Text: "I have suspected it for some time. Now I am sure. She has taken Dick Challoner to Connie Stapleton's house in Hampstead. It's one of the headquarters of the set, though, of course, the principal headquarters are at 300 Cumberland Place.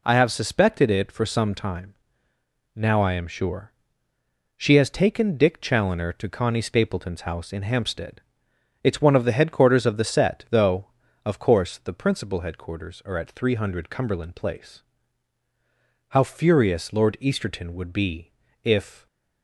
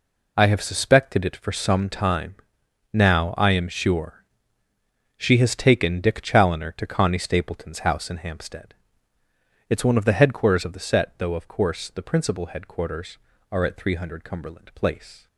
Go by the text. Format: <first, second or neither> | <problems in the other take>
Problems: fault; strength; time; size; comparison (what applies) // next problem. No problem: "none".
second | goes on to say "How furious Lord Easterton would be if"; strong; from 16.1 s on; 2.9 s long